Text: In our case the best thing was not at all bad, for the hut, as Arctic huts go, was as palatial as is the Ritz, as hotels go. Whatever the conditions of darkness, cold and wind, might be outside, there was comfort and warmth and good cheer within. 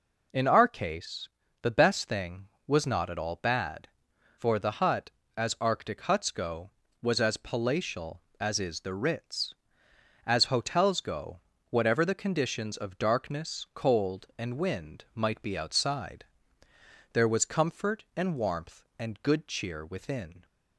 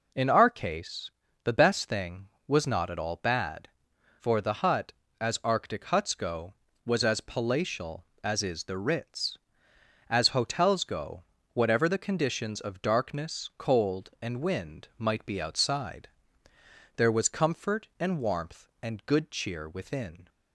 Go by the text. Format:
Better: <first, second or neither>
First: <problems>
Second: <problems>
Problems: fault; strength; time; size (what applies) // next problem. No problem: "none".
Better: neither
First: pauses between "case" and "the"; slight; at 1.2 s; 0.34 s long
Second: pauses between "case" and "the"; slight; at 1.1 s; 0.34 s long